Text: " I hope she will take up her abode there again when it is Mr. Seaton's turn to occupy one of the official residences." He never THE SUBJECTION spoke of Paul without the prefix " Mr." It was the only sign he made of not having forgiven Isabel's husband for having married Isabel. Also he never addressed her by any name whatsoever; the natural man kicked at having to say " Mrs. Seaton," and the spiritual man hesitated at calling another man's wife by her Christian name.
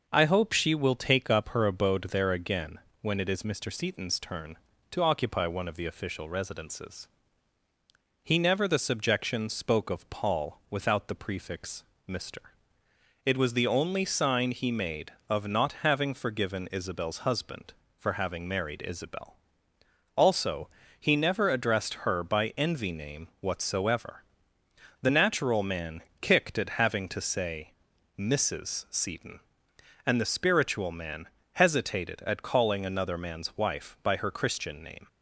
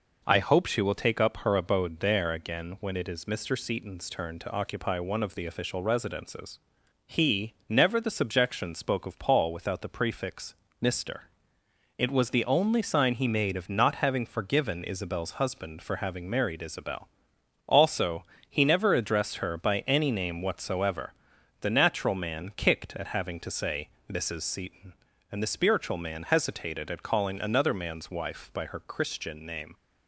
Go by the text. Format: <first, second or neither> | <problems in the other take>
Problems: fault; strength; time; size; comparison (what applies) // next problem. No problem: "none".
second | pauses between "again" and "when"; slight; at 2.7 s; 0.22 s long // pauses between "Also" and "he"; slight; at 20.6 s; 0.32 s long; slight in the second // says "envy" for "any"; at 22.5 s // pauses between "man" and "kicked"; slight; at 26.0 s; 0.20 s long // pauses between "man" and "hesitated"; slight; at 31.2 s; 0.26 s long